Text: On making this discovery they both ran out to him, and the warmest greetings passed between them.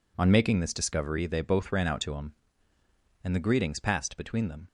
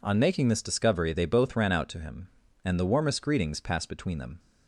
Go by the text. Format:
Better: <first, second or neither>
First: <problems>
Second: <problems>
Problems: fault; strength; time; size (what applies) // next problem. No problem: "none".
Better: second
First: skips "warmest"; at 3.4 s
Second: none